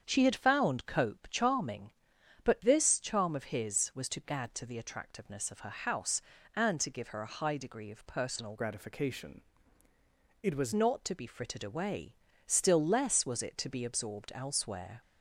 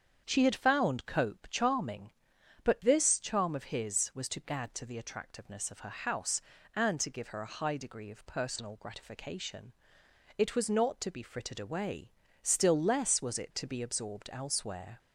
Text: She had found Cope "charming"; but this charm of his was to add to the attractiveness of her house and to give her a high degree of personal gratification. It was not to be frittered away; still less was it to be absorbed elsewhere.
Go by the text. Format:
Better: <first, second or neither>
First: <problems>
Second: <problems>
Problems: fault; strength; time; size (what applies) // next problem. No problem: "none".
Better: second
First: starts louder than the rest; strong; until 1.0 s; 7.5 dB // changes voice from "gratification" to "was"; from 8.5 to 10.7 s; 2.2 s long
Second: starts louder than the rest; strong; until 1.2 s; 7.5 dB